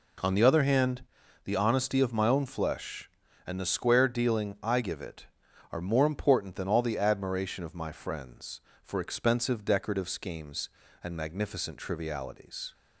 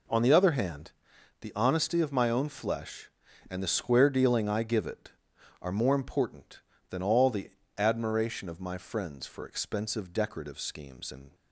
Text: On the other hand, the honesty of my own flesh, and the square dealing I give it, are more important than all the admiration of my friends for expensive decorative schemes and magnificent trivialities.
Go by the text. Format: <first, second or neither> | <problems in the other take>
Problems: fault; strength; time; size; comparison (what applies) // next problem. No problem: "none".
first | pauses between "the" and "admiration"; slight; at 7.4 s; 0.30 s long // stops before "magnificent trivialities"; at 11.3 s